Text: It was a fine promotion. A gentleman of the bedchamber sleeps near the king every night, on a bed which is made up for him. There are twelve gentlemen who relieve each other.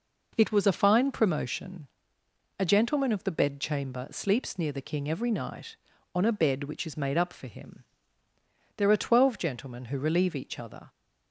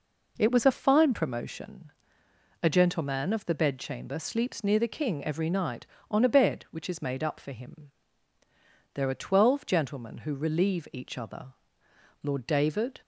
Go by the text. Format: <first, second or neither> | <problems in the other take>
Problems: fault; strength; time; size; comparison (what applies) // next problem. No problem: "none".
first | goes on to say "Lord David"; noticeable; from 12.2 s on; 0.80 s long